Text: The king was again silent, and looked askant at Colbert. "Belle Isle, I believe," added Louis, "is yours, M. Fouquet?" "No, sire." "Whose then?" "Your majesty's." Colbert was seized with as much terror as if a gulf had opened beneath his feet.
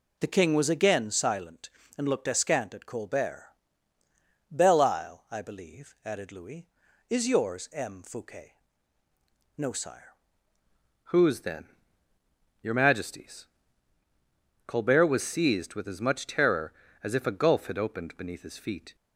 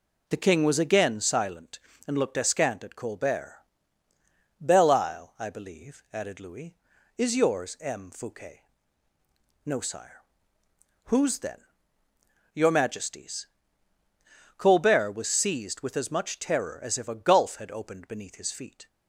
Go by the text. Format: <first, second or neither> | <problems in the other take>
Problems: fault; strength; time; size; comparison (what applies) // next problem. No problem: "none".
second | changes voice at "Whose"; from 11.0 s on; 7.9 s long